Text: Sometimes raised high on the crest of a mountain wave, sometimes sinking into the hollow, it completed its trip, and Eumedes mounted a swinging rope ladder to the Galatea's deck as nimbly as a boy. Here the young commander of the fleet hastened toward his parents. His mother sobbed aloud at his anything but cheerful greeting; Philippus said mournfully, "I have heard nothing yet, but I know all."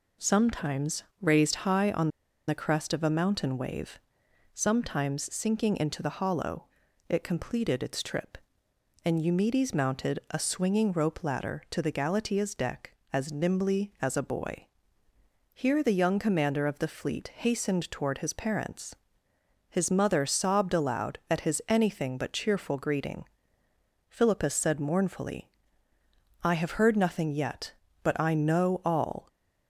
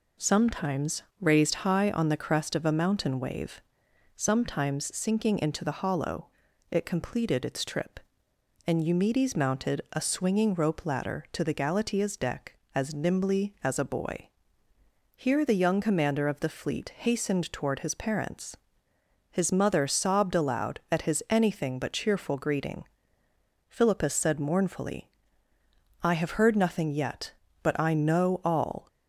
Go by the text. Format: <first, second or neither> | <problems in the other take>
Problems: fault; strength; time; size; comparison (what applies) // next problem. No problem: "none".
second | pauses between "Sometimes" and "raised"; slight; at 1.0 s; 0.16 s long; slight in the second // pauses between "on" and "the"; at 2.0 s; 0.39 s long